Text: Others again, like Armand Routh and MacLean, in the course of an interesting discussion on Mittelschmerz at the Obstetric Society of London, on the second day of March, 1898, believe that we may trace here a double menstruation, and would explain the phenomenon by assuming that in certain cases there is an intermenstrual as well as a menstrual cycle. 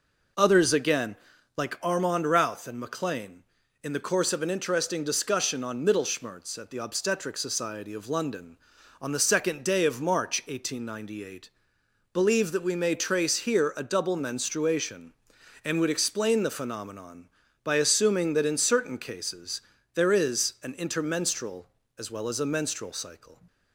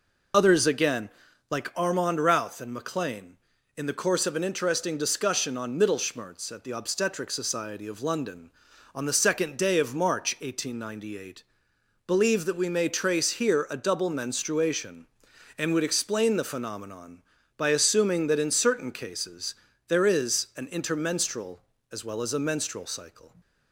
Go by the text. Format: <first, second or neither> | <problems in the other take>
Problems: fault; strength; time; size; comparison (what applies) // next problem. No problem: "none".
first | loses the start of "Others"; at 0.3 s; 45 ms // pauses between "cases" and "there"; slight; at 19.5 s; 0.34 s long; slight in the first